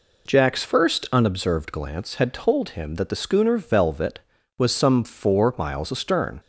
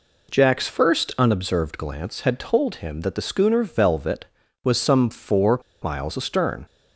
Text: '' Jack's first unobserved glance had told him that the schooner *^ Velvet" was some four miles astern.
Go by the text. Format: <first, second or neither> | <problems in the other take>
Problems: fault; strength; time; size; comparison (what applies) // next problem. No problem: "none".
first | pauses between "four" and "miles"; slight; at 5.5 s; 0.23 s long